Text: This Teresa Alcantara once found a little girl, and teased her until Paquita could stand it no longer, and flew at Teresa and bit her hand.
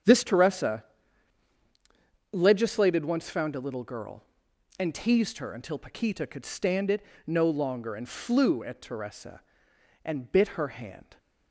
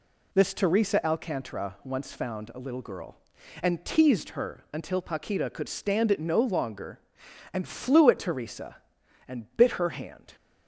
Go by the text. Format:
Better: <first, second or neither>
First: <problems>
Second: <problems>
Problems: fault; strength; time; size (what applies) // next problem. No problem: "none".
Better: second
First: starts louder than the rest; strong; until 2.5 s; 8.5 dB // says "Legislated" for "Alcantara"; at 2.3 s // pauses between "it" and "no"; slight; at 7.0 s; 0.22 s long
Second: none